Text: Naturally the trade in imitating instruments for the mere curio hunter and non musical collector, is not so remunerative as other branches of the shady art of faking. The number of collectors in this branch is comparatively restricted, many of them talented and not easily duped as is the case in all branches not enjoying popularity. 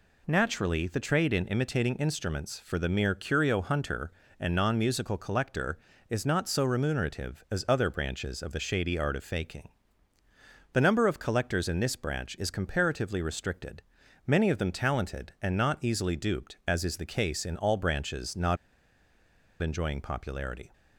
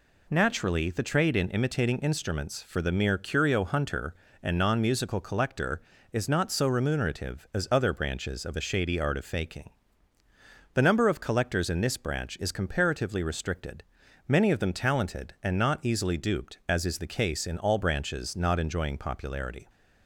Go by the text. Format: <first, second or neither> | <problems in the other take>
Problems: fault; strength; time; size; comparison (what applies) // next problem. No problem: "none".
second | pauses between "not" and "enjoying"; at 18.5 s; 1.0 s long